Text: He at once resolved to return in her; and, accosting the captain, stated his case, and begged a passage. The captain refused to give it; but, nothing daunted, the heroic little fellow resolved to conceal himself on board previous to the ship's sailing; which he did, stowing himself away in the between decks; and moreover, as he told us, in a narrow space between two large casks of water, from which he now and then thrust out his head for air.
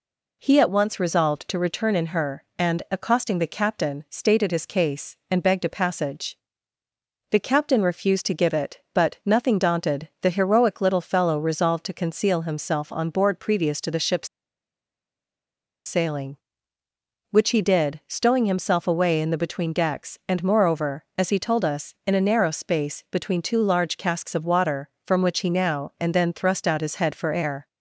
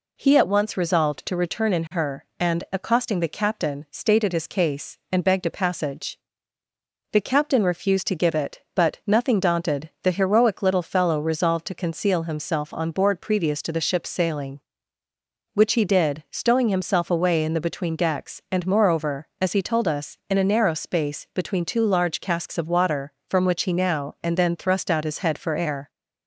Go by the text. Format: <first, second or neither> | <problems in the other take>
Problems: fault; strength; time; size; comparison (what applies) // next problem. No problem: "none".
second | pauses between "ship's" and "sailing"; strong; at 14.2 s; 1.5 s long